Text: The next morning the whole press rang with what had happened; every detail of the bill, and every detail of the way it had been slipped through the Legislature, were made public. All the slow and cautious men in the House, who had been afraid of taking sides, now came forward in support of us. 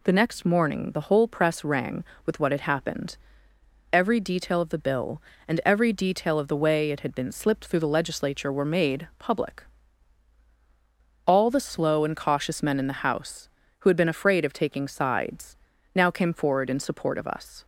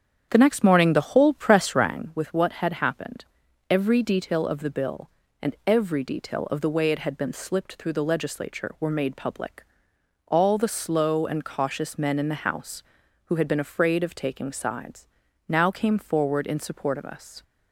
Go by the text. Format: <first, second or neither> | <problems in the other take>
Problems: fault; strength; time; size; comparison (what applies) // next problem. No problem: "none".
first | starts louder than the rest; strong; until 2.0 s; 8.5 dB